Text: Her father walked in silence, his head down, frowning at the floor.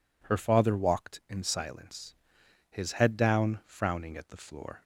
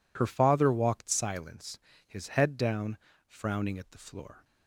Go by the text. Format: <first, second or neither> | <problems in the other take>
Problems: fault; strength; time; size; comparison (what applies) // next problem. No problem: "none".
first | skips "in"; at 1.1 s